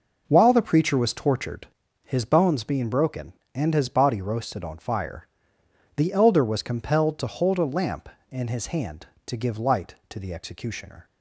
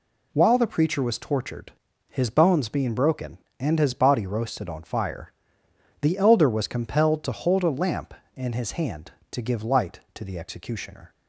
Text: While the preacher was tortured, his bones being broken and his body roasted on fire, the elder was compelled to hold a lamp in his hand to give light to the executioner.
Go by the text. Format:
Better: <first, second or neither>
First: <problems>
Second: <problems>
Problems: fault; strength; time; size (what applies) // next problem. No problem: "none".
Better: second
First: starts louder than the rest; noticeable; until 1.8 s; 5.5 dB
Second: none